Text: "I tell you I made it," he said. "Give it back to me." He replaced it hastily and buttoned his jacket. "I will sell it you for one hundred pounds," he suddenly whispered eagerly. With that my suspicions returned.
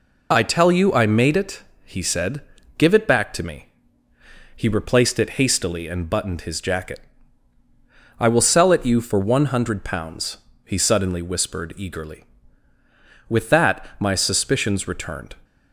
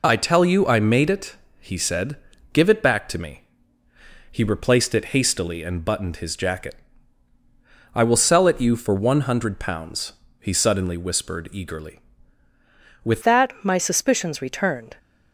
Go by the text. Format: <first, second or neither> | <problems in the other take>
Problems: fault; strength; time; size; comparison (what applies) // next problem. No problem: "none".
first | changes voice at "that"; from 13.2 s on; 1.7 s long